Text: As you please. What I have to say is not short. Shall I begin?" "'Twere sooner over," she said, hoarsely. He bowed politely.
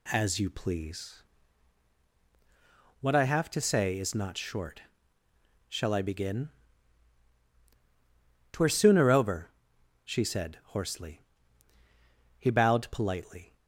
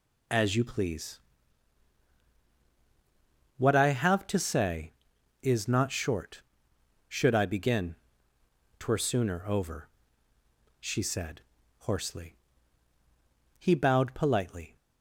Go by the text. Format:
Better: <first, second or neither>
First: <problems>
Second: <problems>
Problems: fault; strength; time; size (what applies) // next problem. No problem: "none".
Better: first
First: none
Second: says "Should" for "Shall"; at 7.0 s